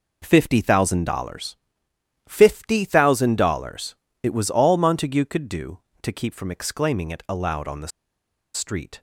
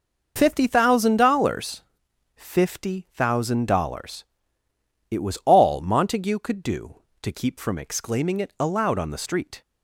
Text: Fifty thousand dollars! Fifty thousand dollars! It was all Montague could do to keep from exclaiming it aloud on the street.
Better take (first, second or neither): second